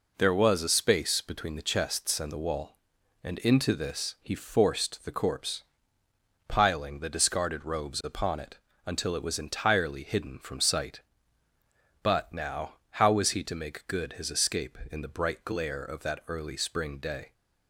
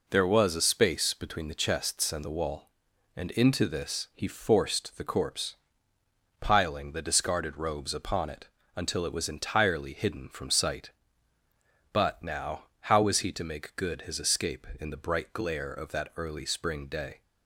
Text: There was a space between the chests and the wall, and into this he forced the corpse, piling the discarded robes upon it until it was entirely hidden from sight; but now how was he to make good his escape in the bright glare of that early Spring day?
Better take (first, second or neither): neither